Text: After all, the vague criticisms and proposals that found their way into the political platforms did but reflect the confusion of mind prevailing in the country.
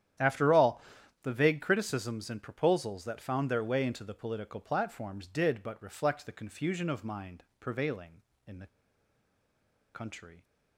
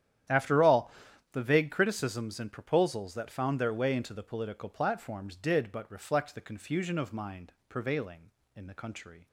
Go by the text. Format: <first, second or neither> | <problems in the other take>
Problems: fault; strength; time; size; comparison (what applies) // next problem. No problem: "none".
second | starts louder than the rest; strong; until 1.6 s; 10 dB; strong in the second // pauses between "mind" and "prevailing"; slight; at 7.4 s; 0.16 s long; slight in the second // pauses between "the" and "country"; strong; at 8.6 s; 1.2 s long